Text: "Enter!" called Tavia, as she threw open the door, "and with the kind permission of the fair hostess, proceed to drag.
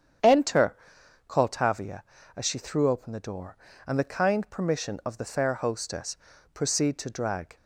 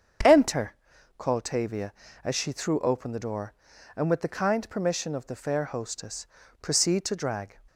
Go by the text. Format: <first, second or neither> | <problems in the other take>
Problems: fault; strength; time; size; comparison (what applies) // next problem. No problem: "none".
second | starts louder than the rest; strong; until 1.7 s; 8.5 dB; also in the second // skips "with"; at 3.9 s